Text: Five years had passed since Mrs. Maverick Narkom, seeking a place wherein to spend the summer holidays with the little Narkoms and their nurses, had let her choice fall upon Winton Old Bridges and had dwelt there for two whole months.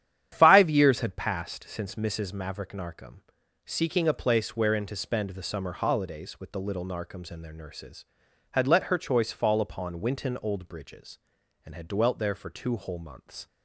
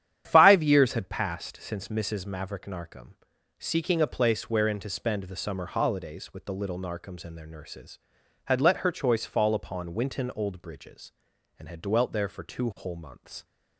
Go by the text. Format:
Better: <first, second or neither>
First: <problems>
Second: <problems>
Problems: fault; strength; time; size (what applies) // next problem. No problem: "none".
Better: neither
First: starts louder than the rest; strong; until 1.3 s; 10 dB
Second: starts louder than the rest; strong; until 1.3 s; 10 dB